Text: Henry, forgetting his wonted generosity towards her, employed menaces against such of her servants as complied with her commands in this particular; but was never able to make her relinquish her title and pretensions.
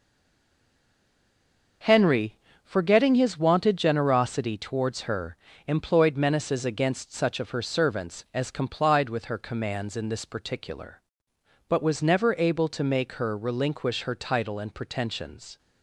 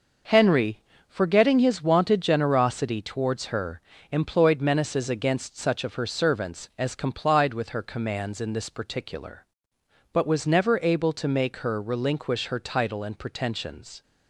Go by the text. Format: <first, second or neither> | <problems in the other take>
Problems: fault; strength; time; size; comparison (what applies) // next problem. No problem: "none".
second | stays silent before the first word; noticeable; until 1.8 s; 1.8 s long